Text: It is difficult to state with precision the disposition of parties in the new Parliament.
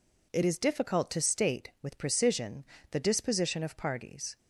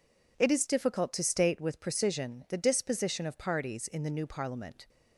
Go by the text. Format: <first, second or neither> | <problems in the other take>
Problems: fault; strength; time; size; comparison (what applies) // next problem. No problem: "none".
second | pauses between "precision" and "the"; slight; at 2.6 s; 0.24 s long // stops before "in the new Parliament"; at 4.3 s